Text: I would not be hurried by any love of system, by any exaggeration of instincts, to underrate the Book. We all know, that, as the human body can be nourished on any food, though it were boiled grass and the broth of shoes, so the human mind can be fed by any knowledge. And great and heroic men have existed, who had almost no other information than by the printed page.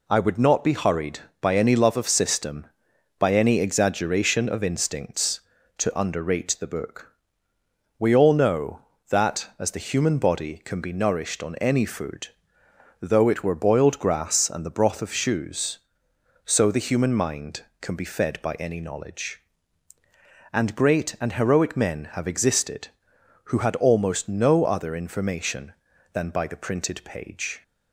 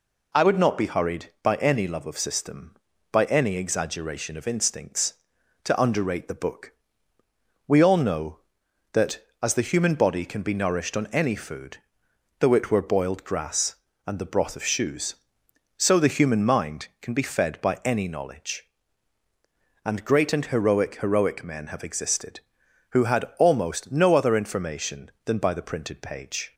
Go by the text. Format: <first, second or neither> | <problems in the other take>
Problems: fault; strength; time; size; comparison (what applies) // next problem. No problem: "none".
first | says "heroic" twice; at 21.0 s